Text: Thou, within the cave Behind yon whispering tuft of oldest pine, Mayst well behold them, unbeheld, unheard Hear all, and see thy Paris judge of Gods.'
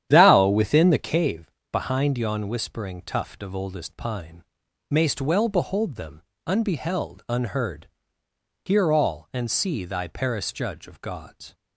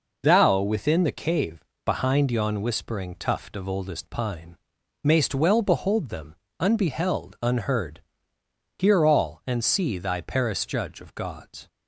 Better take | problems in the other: second | starts louder than the rest; strong; until 1.4 s; 10 dB // pauses between "cave" and "Behind"; slight; at 1.5 s; 0.22 s long; slight in the second // pauses between "unheard" and "Hear"; noticeable; at 7.8 s; 0.78 s long; noticeable in the second

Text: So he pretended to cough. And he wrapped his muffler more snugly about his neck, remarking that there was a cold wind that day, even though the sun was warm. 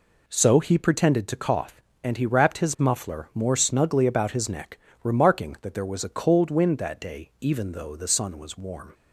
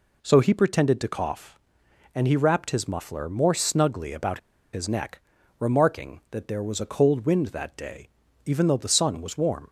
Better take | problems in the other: first | pauses between "about" and "his"; slight; at 4.3 s; 0.33 s long

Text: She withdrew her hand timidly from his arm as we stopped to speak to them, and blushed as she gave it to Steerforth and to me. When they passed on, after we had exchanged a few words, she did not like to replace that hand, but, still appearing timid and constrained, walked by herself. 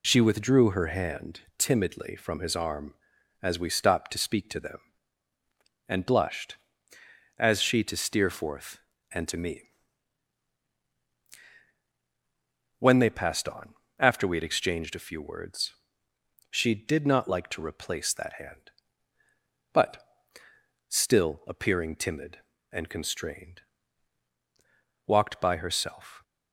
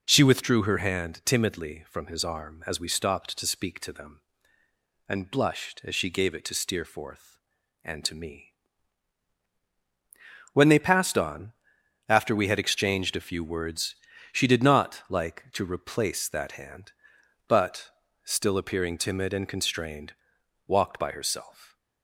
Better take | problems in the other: second | pauses between "hand" and "timidly"; slight; at 1.3 s; 0.18 s long // skips "gave it"; at 7.8 s

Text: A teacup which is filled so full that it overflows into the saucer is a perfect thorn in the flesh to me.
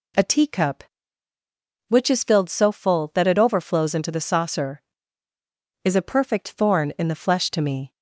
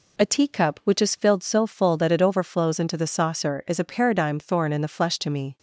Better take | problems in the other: first | says "paradigm" for "perfect"; at 3.8 s

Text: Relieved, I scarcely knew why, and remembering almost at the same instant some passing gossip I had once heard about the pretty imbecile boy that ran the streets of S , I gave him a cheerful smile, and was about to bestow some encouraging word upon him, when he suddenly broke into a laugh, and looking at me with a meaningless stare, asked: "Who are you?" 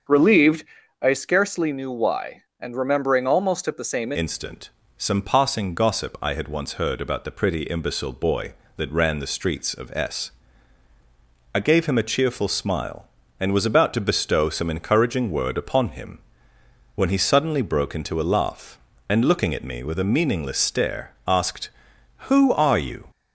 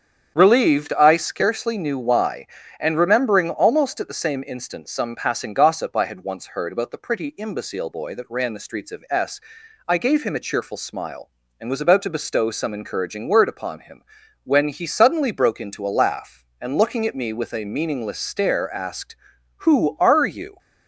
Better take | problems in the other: second | starts louder than the rest; until 1.4 s; 7 dB; strong in the second // changes voice at "instant"; from 4.1 s on; 18.9 s long // pauses between "instant" and "some"; slight; at 4.6 s; 0.30 s long

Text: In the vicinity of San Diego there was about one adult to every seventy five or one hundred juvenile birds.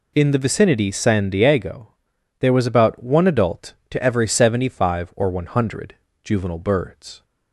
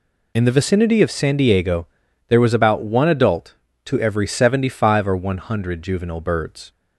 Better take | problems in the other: second | skips "of"; at 0.9 s // pauses between "Diego" and "there"; noticeable; at 1.8 s; 0.50 s long; also in the second // pauses between "hundred" and "juvenile"; slight; at 5.9 s; 0.26 s long

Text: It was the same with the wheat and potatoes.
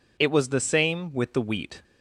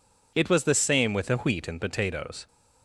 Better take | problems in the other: second | stops before "and potatoes"; at 1.8 s

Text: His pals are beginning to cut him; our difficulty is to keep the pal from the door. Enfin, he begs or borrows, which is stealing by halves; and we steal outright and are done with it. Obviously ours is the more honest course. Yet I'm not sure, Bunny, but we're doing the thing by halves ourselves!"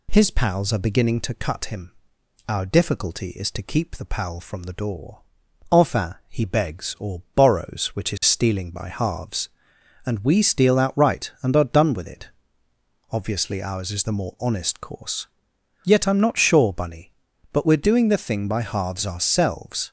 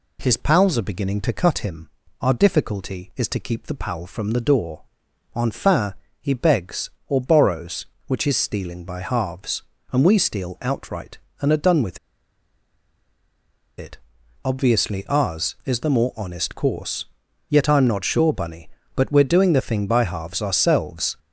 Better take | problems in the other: first | pauses between "with" and "it"; strong; at 11.9 s; 1.8 s long

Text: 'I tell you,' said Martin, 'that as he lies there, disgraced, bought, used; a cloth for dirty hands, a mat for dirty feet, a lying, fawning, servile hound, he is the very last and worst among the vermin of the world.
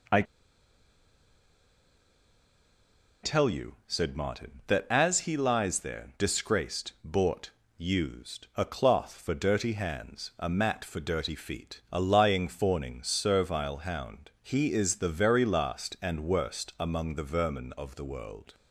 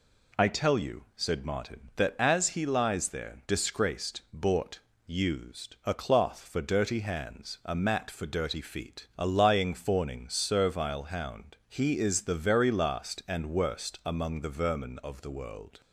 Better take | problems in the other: second | pauses between "I" and "tell"; strong; at 0.2 s; 3.0 s long

